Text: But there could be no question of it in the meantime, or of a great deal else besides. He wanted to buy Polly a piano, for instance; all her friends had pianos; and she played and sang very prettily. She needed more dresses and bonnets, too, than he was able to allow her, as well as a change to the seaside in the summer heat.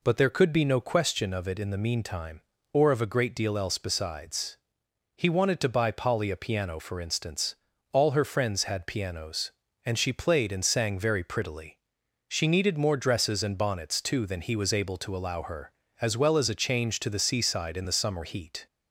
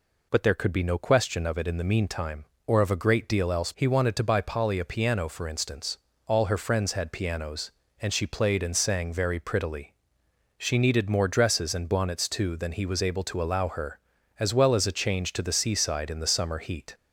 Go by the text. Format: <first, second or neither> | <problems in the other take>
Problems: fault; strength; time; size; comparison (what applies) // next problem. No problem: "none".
first | skips "besides"; at 3.7 s